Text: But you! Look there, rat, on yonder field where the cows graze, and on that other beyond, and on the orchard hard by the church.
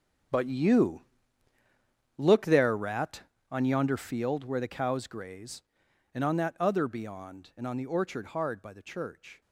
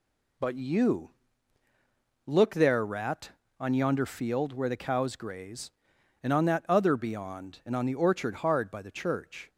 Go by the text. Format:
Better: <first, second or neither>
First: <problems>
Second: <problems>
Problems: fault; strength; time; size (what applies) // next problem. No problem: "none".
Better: second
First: gets quieter; strong; throughout; 14 dB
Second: none